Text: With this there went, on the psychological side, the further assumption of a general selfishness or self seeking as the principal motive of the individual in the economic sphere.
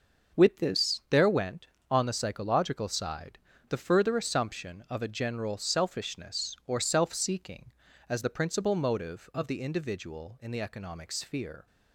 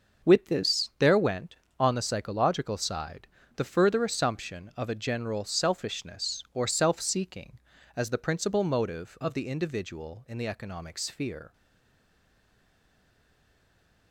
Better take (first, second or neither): first